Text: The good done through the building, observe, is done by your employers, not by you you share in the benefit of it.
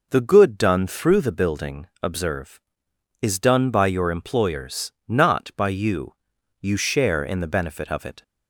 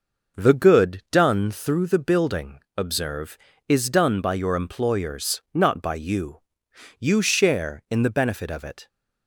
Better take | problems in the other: first | gets quieter; throughout; 6.5 dB // pauses between "you" and "you"; noticeable; at 6.4 s; 0.58 s long; noticeable in the first

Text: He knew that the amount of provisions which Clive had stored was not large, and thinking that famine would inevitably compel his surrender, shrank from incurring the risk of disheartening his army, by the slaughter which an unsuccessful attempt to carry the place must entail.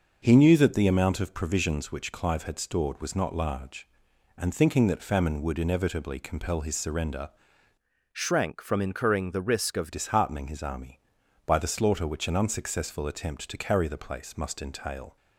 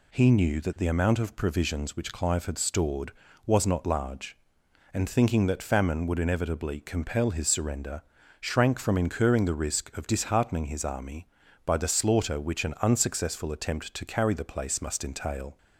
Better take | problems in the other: second | starts louder than the rest; until 1.2 s; 6 dB // changes voice from "shrank" to "of"; from 8.1 to 9.9 s; 1.8 s long

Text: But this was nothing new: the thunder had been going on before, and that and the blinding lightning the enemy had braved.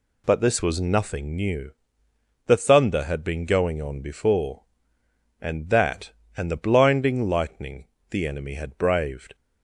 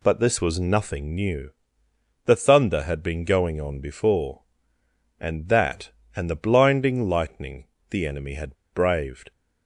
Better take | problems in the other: first | pauses between "lightning" and "the"; slight; at 7.6 s; 0.22 s long; slight in the first // pauses between "had" and "braved"; slight; at 8.5 s; 0.19 s long

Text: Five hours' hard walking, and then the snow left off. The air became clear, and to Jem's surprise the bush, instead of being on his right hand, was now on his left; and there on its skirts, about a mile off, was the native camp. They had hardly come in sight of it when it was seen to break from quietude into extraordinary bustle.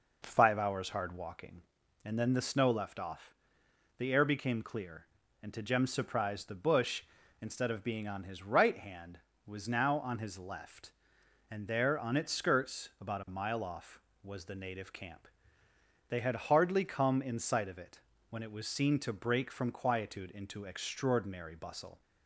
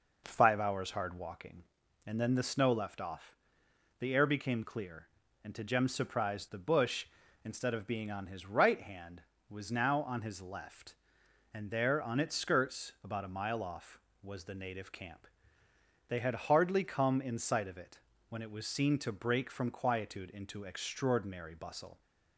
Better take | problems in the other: neither | pauses between "it" and "when"; slight; the same in both

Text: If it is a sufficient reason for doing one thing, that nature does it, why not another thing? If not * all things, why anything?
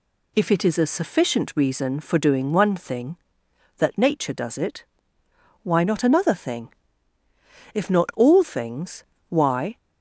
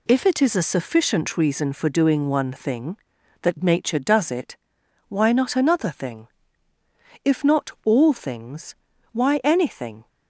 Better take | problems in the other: second | stops before "anything"; at 9.7 s

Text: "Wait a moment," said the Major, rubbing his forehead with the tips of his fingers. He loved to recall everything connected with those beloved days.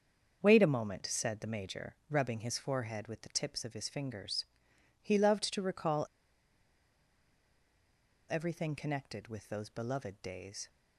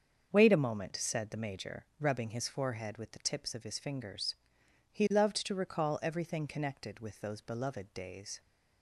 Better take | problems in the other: second | starts louder than the rest; until 1.4 s; 7 dB; also in the second // pauses between "recall" and "everything"; strong; at 6.0 s; 2.2 s long

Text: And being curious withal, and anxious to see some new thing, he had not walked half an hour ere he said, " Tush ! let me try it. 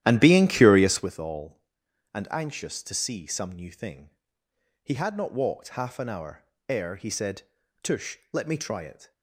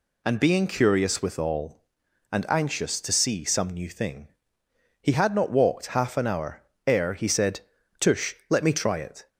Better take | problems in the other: second | starts louder than the rest; strong; until 1.2 s; 12.5 dB // pauses between "hour" and "ere"; slight; at 6.4 s; 0.26 s long; slight in the second

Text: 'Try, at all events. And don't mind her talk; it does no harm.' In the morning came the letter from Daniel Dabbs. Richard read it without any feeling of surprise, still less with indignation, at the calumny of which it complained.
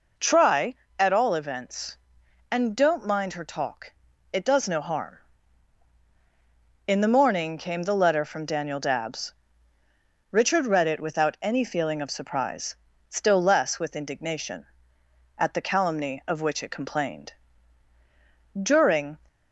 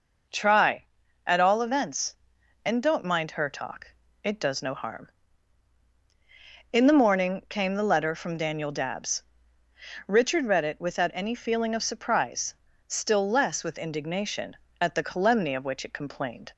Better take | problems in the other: second | goes on to say "During"; from 18.5 s on; 0.60 s long

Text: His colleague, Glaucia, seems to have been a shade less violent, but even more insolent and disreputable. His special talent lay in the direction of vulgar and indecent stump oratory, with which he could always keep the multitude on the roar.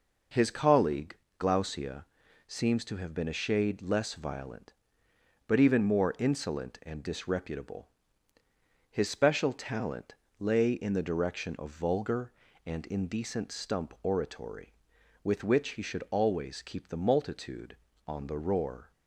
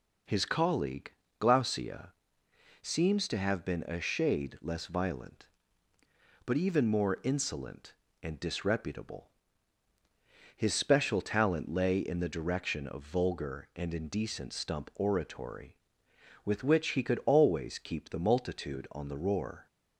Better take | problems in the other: second | pauses between "talent" and "lay"; slight; at 10.1 s; 0.26 s long // says "should" for "could"; at 15.8 s

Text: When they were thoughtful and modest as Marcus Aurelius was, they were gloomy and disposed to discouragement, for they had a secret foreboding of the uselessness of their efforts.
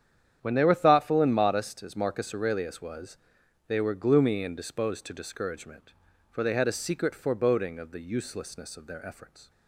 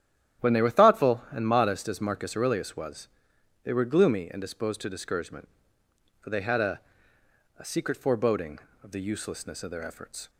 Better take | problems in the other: first | starts louder than the rest; strong; until 1.5 s; 11 dB; strong in the first // says "a" twice; at 7.5 s

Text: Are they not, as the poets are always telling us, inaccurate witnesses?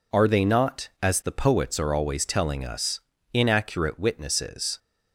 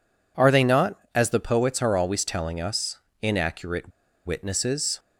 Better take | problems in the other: first | pauses between "inaccurate" and "witnesses"; slight; at 3.9 s; 0.36 s long

